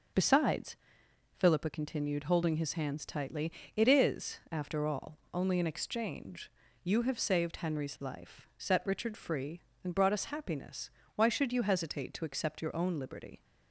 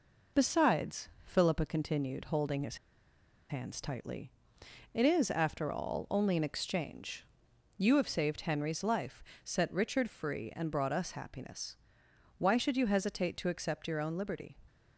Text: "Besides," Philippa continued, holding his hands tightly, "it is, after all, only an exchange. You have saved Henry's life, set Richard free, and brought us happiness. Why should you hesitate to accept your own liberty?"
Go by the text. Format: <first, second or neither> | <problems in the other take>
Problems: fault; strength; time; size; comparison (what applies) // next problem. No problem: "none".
first | pauses between "his" and "hands"; noticeable; at 2.7 s; 0.74 s long